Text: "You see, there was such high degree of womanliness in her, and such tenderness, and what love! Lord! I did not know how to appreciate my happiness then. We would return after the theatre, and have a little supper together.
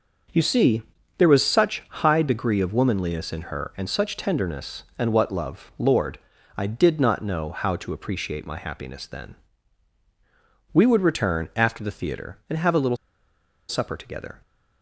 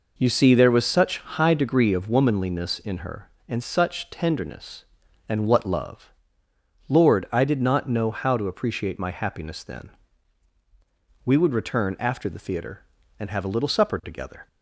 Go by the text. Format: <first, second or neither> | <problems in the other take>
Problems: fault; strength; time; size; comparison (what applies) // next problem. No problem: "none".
second | starts louder than the rest; until 1.6 s; 6.5 dB // pauses between "little" and "supper"; noticeable; at 12.9 s; 0.72 s long